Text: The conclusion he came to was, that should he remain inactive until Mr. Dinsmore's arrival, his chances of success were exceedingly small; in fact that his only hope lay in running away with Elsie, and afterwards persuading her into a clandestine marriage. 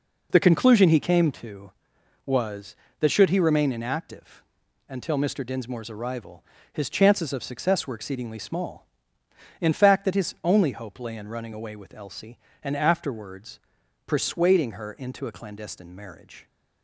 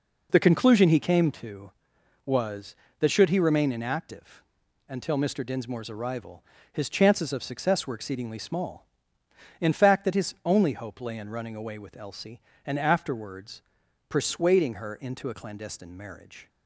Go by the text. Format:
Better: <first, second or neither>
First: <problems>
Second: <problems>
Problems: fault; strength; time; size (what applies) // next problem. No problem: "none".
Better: neither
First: pauses between "inactive" and "until"; at 4.4 s; 0.44 s long // pauses between "afterwards" and "persuading"; noticeable; at 13.5 s; 0.46 s long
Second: pauses between "inactive" and "until"; at 4.4 s; 0.44 s long // pauses between "afterwards" and "persuading"; noticeable; at 13.6 s; 0.46 s long